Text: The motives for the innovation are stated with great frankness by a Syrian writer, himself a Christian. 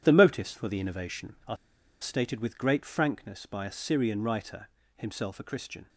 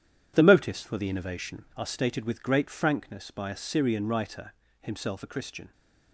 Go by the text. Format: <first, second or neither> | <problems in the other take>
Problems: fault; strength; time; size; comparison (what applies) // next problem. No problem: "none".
second | pauses between "are" and "stated"; at 1.5 s; 0.45 s long